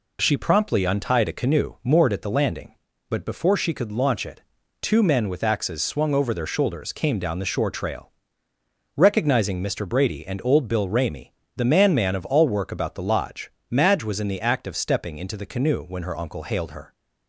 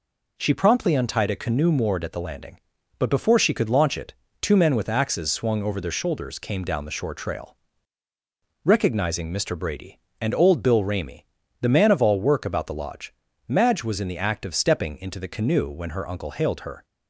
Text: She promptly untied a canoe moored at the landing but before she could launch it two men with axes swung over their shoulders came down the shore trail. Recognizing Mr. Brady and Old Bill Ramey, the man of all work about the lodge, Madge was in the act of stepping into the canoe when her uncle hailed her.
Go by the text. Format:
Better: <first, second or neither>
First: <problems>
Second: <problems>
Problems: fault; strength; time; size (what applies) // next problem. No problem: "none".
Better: second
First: pauses between "it" and "two"; at 4.4 s; 0.40 s long // says "man" twice; at 11.9 s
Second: pauses between "it" and "two"; slight; at 4.1 s; 0.26 s long